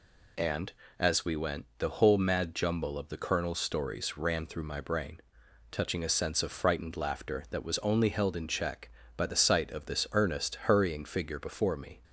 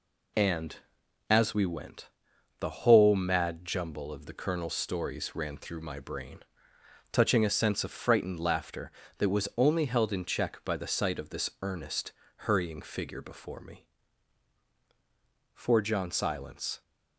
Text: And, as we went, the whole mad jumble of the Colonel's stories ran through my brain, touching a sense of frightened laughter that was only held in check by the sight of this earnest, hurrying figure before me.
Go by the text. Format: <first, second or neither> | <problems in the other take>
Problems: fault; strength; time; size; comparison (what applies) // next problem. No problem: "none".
first | goes on to say "For John Silence"; noticeable; from 15.5 s on; 1.2 s long